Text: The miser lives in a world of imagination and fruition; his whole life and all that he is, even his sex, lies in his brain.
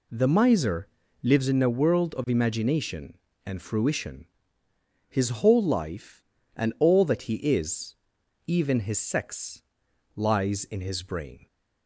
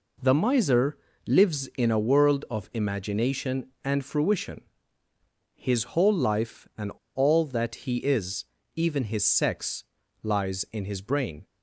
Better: first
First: pauses between "miser" and "lives"; slight; at 0.8 s; 0.34 s long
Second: pauses between "miser" and "lives"; slight; at 0.9 s; 0.30 s long // pauses between "and" and "all"; slight; at 6.9 s; 0.25 s long

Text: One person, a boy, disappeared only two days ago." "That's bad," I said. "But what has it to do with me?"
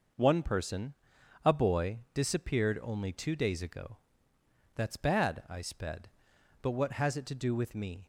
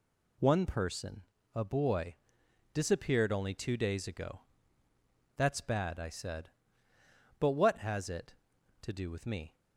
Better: second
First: says "sped" for "said"; at 5.6 s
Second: none

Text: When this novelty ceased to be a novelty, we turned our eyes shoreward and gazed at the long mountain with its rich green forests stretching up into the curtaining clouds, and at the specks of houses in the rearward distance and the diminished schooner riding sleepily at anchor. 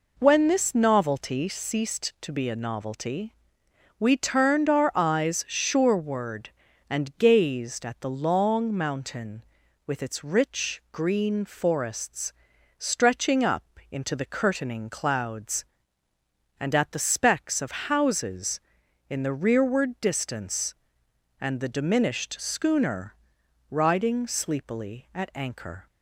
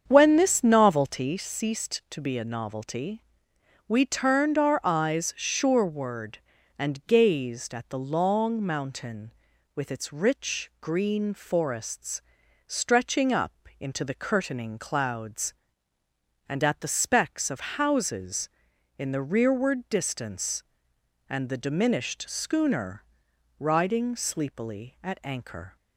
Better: first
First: pauses between "forests" and "stretching"; noticeable; at 12.3 s; 0.46 s long // pauses between "up" and "into"; slight; at 13.6 s; 0.26 s long // pauses between "schooner" and "riding"; noticeable; at 23.1 s; 0.56 s long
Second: starts louder than the rest; strong; until 1.3 s; 7.5 dB // pauses between "forests" and "stretching"; noticeable; at 12.2 s; 0.46 s long // pauses between "up" and "into"; slight; at 13.5 s; 0.26 s long // pauses between "schooner" and "riding"; noticeable; at 23.0 s; 0.56 s long

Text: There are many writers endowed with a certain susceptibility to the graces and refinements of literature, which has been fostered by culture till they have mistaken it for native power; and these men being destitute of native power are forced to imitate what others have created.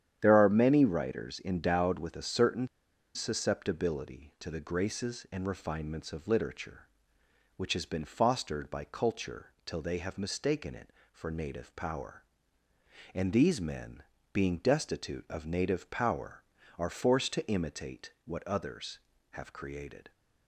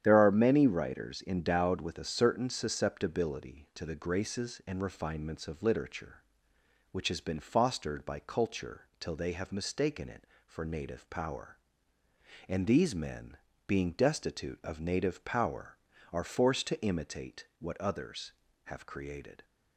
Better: second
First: starts louder than the rest; strong; until 1.2 s; 9.5 dB // pauses between "certain" and "susceptibility"; noticeable; at 2.6 s; 0.47 s long // pauses between "men" and "being"; slight; at 14.0 s; 0.28 s long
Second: starts louder than the rest; strong; until 1.0 s; 9.5 dB // pauses between "men" and "being"; slight; at 13.3 s; 0.28 s long

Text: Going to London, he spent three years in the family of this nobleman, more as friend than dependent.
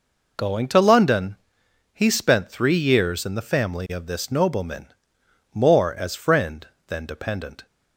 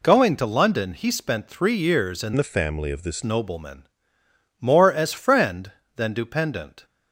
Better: first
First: none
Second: changes voice from "the" to "this"; from 2.3 to 3.2 s; 0.9 s long

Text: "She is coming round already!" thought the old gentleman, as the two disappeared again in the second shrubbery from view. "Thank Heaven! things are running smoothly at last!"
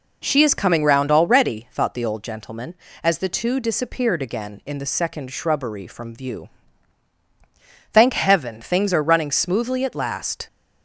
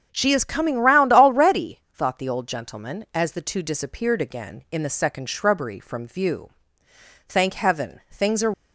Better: first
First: none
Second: starts louder than the rest; strong; until 1.1 s; 7.5 dB // stops before "running smoothly at last"; at 8.5 s

